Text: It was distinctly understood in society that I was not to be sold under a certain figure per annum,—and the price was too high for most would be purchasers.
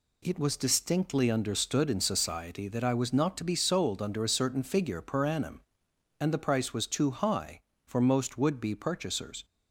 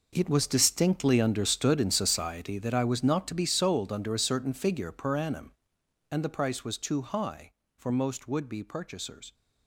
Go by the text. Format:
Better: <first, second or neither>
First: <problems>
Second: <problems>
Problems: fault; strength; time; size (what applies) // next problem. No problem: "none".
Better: first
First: none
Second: gets quieter; strong; throughout; 13.5 dB